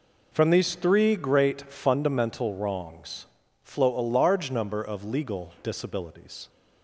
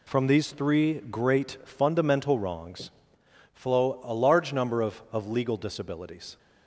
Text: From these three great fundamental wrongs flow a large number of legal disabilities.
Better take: first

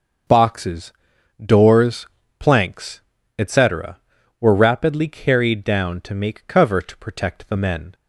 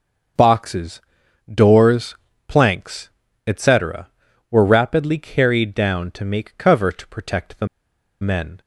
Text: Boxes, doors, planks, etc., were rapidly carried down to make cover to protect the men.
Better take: first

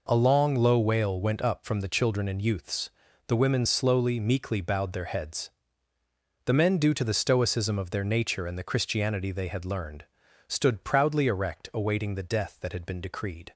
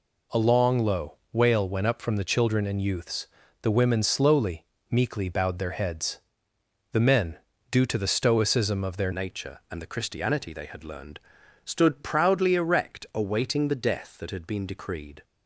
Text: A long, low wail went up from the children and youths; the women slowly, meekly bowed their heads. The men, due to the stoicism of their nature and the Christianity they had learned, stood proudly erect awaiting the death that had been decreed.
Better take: first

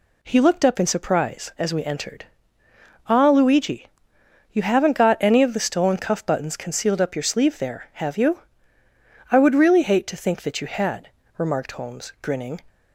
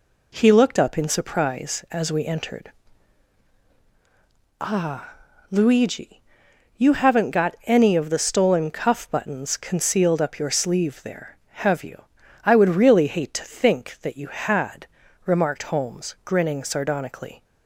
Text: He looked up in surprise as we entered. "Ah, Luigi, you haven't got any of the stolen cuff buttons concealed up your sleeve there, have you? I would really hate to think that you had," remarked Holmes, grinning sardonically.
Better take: second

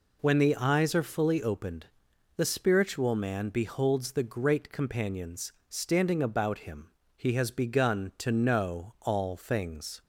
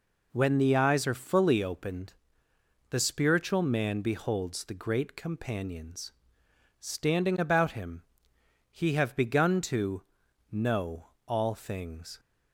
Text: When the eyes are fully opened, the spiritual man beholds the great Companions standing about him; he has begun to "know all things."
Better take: first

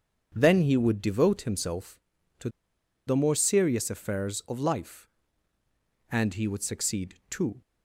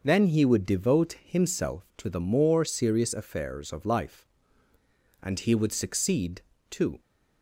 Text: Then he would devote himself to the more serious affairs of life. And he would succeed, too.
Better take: second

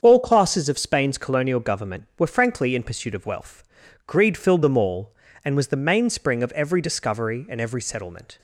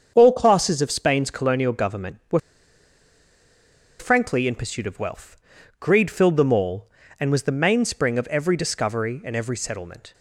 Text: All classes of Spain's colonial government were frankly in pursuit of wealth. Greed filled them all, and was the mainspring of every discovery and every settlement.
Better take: first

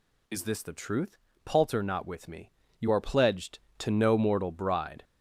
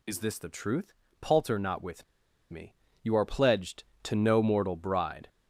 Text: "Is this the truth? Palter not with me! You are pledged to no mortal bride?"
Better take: first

